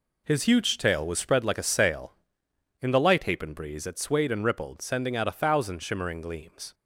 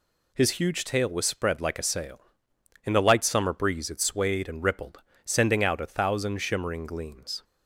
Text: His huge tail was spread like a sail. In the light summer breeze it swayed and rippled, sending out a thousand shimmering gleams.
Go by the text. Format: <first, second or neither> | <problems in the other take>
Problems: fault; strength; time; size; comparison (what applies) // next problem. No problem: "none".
second | says "hapen" for "summer"; at 3.2 s